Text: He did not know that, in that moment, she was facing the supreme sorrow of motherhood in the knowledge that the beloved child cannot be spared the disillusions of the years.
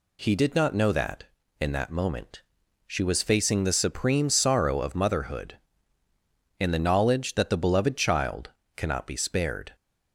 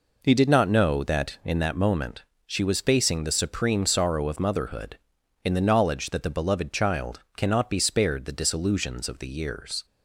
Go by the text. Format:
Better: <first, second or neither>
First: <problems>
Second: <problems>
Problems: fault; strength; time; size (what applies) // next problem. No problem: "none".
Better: second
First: pauses between "child" and "cannot"; slight; at 8.4 s; 0.26 s long // stops before "the disillusions of the years"; at 9.7 s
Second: pauses between "child" and "cannot"; slight; at 7.2 s; 0.16 s long